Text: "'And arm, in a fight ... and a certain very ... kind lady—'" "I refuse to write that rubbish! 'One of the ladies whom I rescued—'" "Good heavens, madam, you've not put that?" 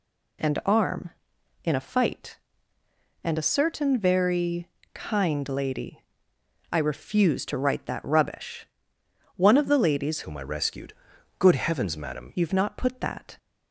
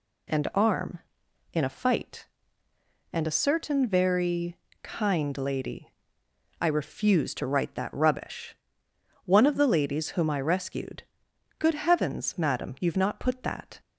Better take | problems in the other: second | changes voice from "whom" to "madam"; from 10.2 to 12.3 s; 2.1 s long

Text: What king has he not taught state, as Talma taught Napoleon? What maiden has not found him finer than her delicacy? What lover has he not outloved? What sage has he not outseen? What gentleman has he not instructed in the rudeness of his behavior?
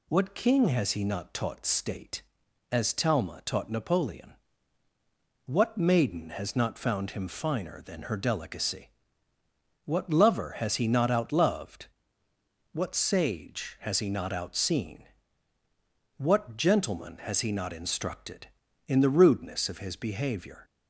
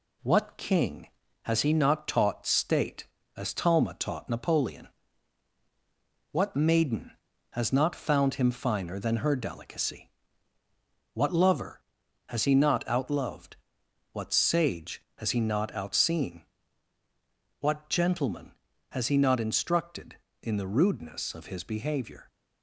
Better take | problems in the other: first | gets quieter; slight; throughout; 2.5 dB

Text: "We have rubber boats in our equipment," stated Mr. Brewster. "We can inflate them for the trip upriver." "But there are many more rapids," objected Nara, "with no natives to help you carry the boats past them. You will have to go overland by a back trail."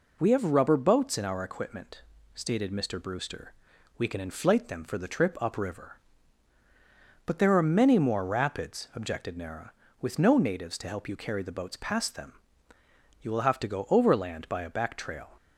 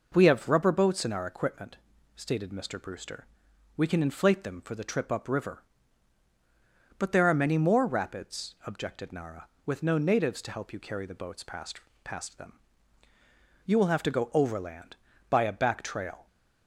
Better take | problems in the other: first | says "past" twice; at 12.0 s

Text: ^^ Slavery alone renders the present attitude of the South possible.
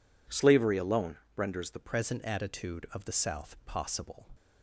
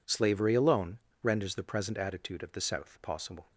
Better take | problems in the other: second | pauses between "alone" and "renders"; slight; at 1.1 s; 0.20 s long; slight in the second // changes voice at "present"; from 1.7 s on; 2.5 s long

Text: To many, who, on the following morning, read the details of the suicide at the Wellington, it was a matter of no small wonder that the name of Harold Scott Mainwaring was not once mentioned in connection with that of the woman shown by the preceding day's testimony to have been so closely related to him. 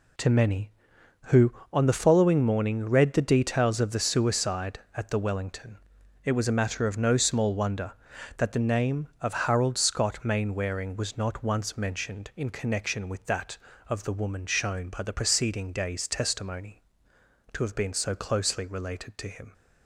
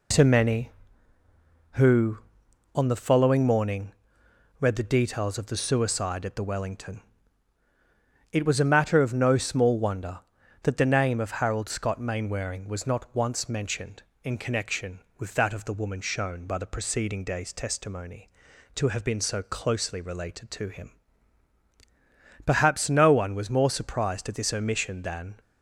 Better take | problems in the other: first | goes on to say "Perhaps no one was more surprised at this omission than"; strong; from 22.4 s on; 2.9 s long

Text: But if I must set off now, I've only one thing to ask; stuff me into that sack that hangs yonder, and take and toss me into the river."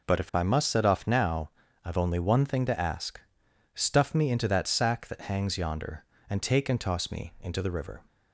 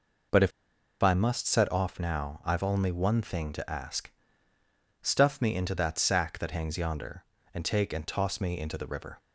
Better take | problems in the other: first | pauses between "if" and "I"; noticeable; at 0.5 s; 0.52 s long

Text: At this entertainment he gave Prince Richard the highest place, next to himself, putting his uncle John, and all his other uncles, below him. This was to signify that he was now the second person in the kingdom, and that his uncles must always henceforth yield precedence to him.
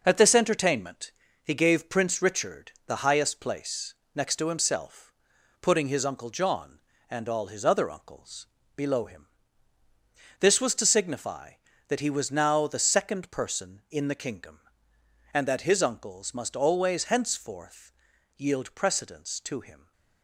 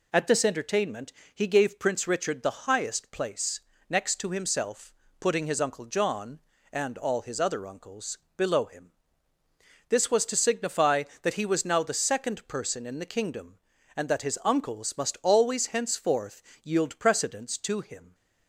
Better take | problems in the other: second | gets quieter; noticeable; throughout; 6 dB // pauses between "entertainment" and "he"; slight; at 1.1 s; 0.32 s long; slight in the second // pauses between "Richard" and "the"; slight; at 2.7 s; 0.16 s long // pauses between "henceforth" and "yield"; noticeable; at 17.9 s; 0.46 s long; slight in the second

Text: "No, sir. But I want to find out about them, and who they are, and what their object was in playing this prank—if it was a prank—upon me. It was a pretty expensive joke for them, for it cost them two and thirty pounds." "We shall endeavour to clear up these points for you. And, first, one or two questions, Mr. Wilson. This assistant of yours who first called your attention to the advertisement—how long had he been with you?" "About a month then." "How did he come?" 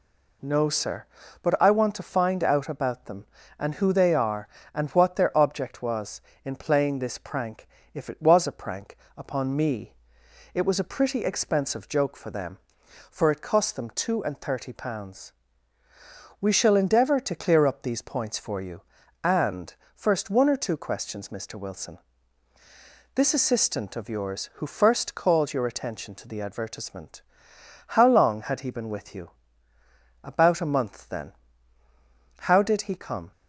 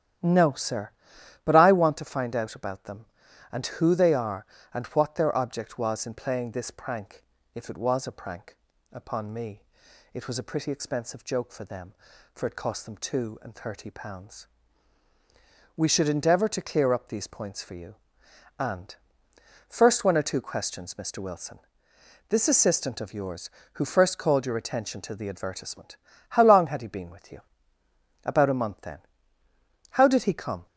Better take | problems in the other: first | starts louder than the rest; strong; until 1.7 s; 11 dB // says "should" for "shall"; at 15.8 s

